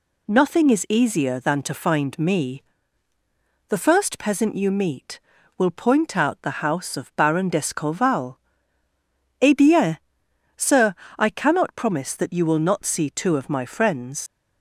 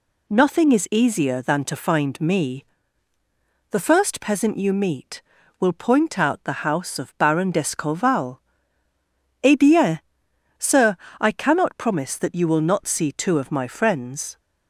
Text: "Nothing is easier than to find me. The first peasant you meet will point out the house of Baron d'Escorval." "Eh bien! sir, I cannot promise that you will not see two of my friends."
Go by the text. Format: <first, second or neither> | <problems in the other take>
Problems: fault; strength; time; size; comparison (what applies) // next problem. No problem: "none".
second | leaves "friends" unfinished; at 14.2 s; 105 ms